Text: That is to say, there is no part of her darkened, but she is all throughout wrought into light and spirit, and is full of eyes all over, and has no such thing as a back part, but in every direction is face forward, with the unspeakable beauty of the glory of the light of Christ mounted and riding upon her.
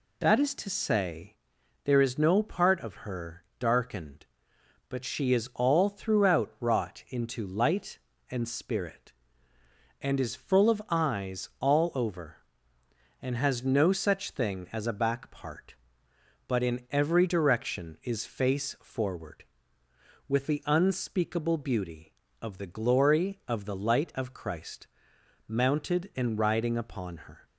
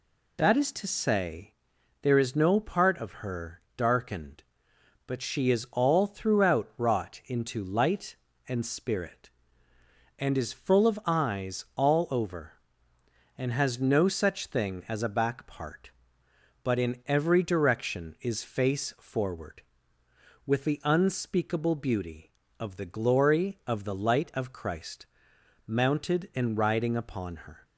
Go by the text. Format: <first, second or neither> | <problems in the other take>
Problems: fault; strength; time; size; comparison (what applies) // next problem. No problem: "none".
neither | pauses between "her" and "darkened"; slight; the same in both // pauses between "Christ" and "mounted"; noticeable; the same in both